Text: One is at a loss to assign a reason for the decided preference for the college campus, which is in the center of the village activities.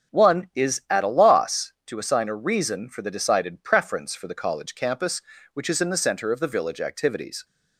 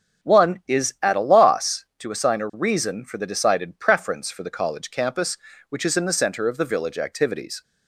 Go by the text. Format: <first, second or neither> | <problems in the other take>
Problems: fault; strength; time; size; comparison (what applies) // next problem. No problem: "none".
neither | starts louder than the rest; strong; the same in both